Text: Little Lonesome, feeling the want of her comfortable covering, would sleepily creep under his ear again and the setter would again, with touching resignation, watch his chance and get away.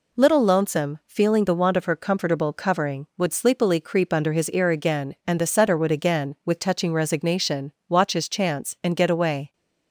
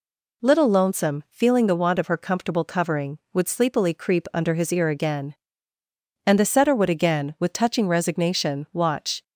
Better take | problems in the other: first | stops before "his chance and get away"; at 9.2 s

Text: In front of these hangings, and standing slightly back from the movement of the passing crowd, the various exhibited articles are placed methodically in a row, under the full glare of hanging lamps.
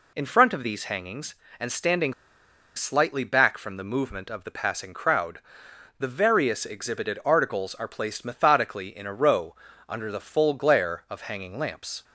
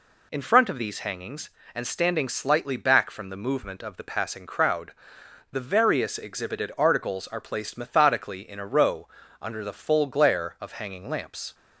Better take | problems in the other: second | pauses between "standing" and "slightly"; noticeable; at 2.1 s; 0.62 s long

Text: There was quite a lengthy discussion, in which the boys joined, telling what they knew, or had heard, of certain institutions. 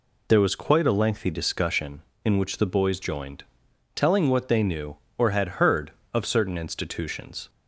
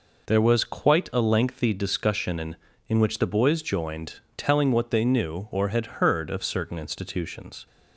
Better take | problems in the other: first | says "in" twice; at 2.8 s

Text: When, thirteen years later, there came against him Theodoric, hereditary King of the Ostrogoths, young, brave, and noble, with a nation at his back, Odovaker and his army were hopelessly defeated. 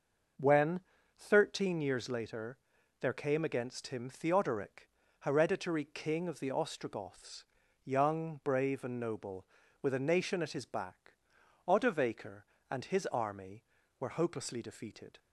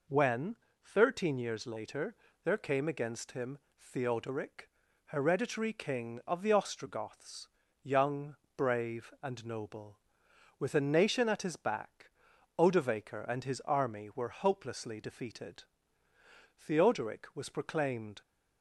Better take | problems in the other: first | pauses between "him" and "Theodoric"; slight; at 3.5 s; 0.20 s long // goes on to say "Theodoric was proclaimed"; from 16.5 s on; 1.6 s long

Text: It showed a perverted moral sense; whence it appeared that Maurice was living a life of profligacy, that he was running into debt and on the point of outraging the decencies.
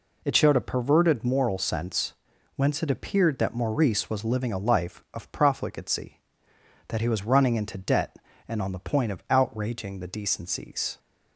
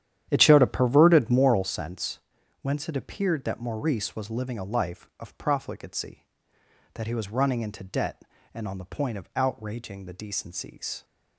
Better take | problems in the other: first | starts louder than the rest; strong; until 1.7 s; 10.5 dB

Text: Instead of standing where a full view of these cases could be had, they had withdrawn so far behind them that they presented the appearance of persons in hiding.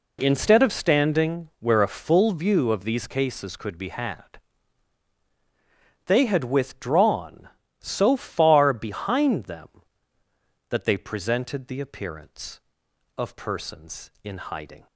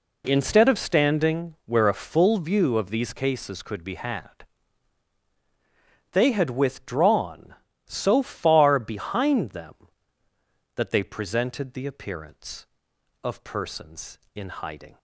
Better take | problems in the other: neither | none

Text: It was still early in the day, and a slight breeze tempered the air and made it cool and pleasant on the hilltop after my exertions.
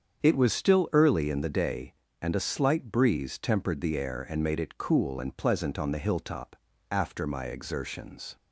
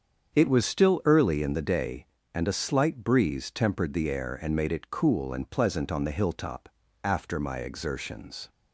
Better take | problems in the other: neither | starts louder than the rest; strong; the same in both // pauses between "hilltop" and "after"; slight; the same in both

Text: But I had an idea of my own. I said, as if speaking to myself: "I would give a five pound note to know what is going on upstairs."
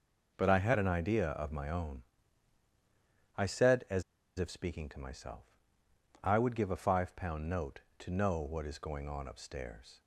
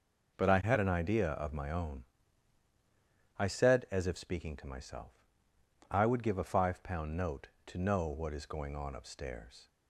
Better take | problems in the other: second | pauses between "as" and "if"; at 4.0 s; 0.36 s long

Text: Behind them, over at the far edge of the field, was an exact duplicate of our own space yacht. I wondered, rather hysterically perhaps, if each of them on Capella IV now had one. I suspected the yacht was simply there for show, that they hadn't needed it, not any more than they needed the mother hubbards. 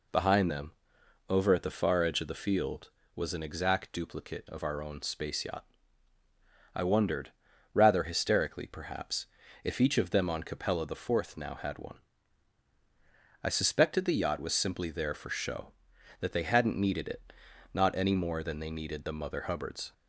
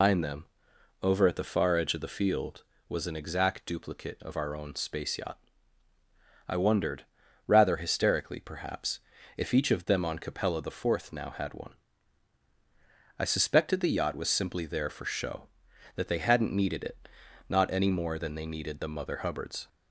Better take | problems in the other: first | loses the start of "Behind"; at 0.0 s; 185 ms

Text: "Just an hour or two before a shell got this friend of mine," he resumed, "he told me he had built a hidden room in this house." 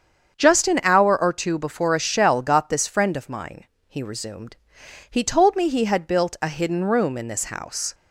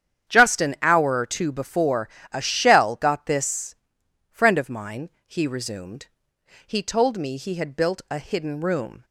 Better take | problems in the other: first | starts louder than the rest; strong; until 1.3 s; 9 dB; strong in the first // pauses between "before" and "a"; slight; at 2.0 s; 0.24 s long // pauses between "this" and "friend"; noticeable; at 3.7 s; 0.54 s long // stops before "in this house"; at 9.0 s

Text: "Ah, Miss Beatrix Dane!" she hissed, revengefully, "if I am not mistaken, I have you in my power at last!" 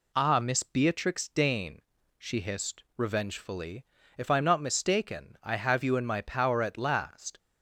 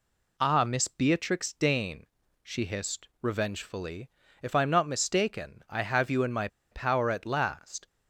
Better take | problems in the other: first | pauses between "my" and "power"; slight; at 6.4 s; 0.24 s long

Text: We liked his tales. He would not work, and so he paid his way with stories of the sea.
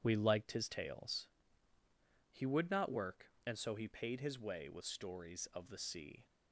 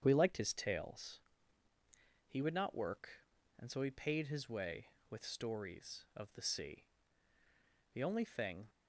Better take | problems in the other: first | starts louder than the rest; strong; until 1.0 s; 8 dB // goes on to say "The only thing"; noticeable; from 7.9 s on; 0.72 s long

